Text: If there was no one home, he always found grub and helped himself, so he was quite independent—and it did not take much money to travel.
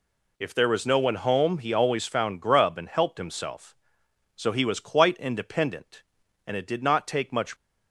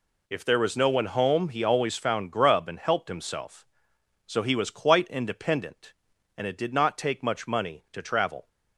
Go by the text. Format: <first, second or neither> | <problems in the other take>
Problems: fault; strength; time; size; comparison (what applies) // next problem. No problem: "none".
second | stops before "money to travel"; at 7.5 s